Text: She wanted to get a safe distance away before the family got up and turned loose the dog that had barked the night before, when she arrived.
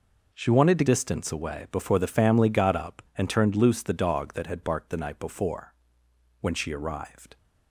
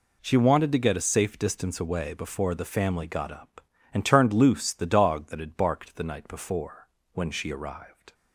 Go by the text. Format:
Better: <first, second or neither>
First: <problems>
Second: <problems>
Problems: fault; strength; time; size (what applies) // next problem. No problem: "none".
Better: second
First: skips "get a safe"; at 0.8 s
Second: none